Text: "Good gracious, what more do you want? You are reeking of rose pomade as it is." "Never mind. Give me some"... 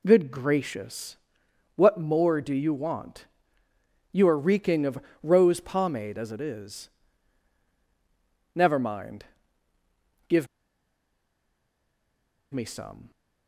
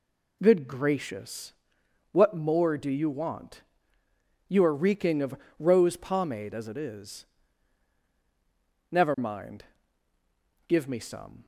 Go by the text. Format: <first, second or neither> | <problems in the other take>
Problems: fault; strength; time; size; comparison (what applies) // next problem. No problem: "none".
second | pauses between "of" and "rose"; slight; at 4.9 s; 0.22 s long; slight in the second // pauses between "Give" and "me"; strong; at 10.4 s; 2.0 s long